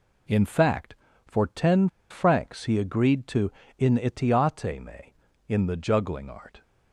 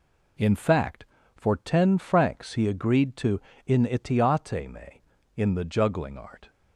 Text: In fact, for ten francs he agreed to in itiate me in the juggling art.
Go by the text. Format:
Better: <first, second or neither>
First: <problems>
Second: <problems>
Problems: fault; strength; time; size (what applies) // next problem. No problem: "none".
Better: second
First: pauses between "ten" and "francs"; slight; at 1.8 s; 0.22 s long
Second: none